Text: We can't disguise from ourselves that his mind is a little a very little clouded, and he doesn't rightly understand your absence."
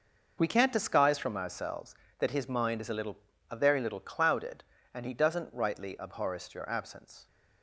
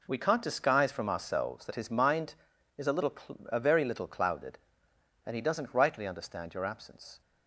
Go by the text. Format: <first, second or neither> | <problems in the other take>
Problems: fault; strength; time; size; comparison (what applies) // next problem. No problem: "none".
second | pauses between "little" and "a"; slight; at 3.1 s; 0.34 s long; slight in the second // says "abhorrest" for "understand"; at 5.9 s